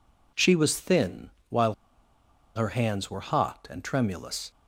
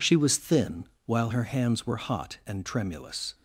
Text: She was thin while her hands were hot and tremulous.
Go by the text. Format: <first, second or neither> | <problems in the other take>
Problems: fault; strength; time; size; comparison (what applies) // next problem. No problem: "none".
second | pauses between "thin" and "while"; slight; at 1.2 s; 0.20 s long; slight in the second // pauses between "while" and "her"; noticeable; at 1.7 s; 0.81 s long